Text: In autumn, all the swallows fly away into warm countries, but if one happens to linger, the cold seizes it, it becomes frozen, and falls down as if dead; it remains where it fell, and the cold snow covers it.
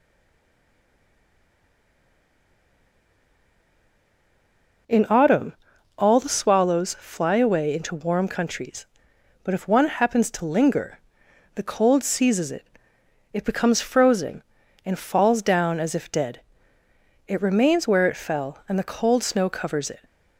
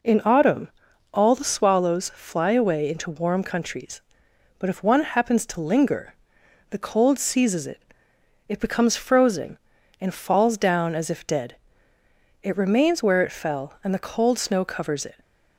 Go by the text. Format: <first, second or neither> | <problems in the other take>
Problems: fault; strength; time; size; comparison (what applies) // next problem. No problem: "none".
second | stays silent before the first word; strong; until 4.8 s; 4.8 s long